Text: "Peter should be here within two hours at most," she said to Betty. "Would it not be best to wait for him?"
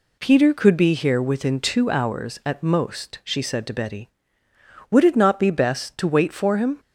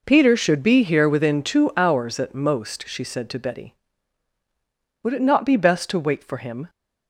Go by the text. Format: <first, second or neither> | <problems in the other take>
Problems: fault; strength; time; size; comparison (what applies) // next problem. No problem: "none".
second | says "could" for "should"; at 0.5 s